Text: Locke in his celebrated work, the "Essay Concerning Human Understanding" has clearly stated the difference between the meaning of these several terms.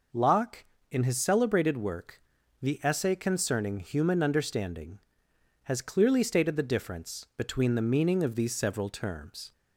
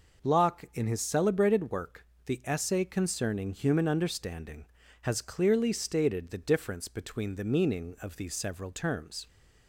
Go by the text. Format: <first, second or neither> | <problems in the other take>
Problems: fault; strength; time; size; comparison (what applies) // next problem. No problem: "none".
neither | none